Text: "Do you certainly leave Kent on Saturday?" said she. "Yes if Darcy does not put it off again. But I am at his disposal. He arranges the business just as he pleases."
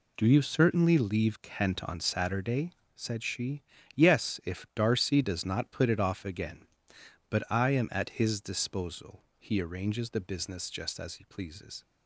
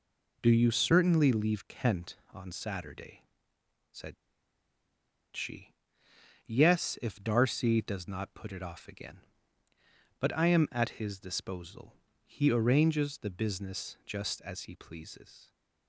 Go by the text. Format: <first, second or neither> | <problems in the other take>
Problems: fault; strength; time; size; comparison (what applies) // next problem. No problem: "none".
first | pauses between "said" and "she"; at 4.1 s; 1.2 s long